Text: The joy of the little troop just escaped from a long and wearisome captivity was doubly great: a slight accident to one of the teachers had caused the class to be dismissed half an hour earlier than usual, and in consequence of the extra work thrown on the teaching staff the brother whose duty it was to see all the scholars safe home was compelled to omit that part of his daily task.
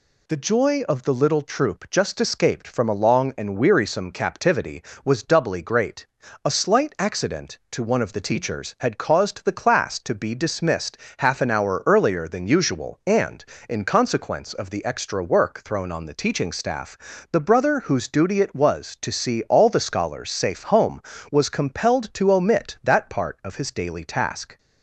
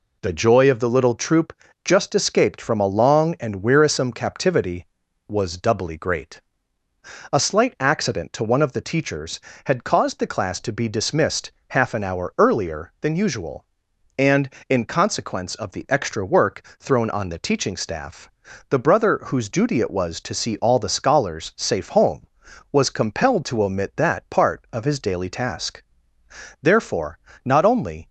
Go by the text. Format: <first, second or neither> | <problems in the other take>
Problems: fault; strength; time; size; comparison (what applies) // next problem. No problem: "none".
first | pauses between "troop" and "just"; slight; at 1.5 s; 0.32 s long // pauses between "dismissed" and "half"; slight; at 11.5 s; 0.16 s long; slight in the first // pauses between "work" and "thrown"; slight; at 16.6 s; 0.18 s long // pauses between "staff" and "the"; at 18.2 s; 0.42 s long; slight in the first // goes on to say "Therefore not only"; from 26.6 s on; 1.4 s long